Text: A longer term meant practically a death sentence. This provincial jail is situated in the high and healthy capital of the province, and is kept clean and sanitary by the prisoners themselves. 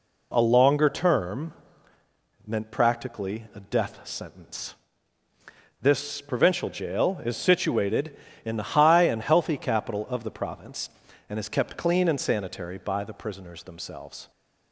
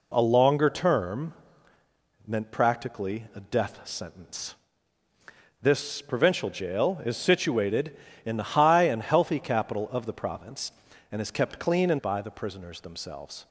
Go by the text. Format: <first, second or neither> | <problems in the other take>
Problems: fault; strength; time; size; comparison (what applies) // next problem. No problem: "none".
first | pauses between "term" and "meant"; noticeable; at 1.3 s; 0.94 s long; noticeable in the first // skips "sanitary"; at 11.9 s